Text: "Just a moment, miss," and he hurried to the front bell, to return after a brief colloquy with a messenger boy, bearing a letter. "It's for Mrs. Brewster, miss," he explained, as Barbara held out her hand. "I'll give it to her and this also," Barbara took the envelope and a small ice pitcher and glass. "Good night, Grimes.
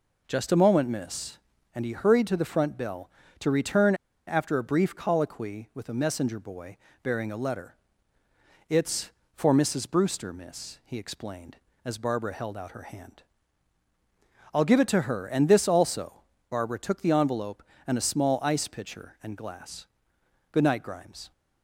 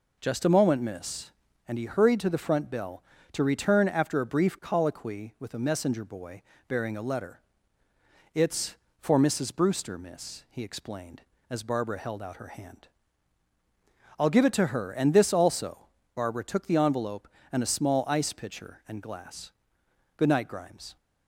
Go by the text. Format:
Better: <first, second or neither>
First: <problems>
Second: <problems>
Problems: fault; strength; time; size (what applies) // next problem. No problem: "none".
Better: second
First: pauses between "return" and "after"; slight; at 3.9 s; 0.32 s long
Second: none